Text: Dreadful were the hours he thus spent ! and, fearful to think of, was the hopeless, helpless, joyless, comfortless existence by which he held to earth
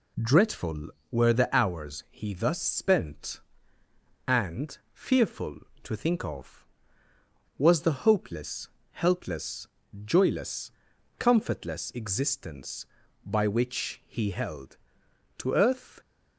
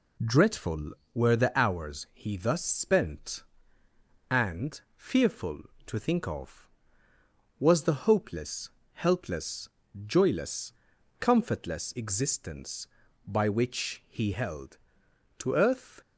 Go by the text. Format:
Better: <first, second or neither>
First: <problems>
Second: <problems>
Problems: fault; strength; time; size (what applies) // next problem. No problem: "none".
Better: neither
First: none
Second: none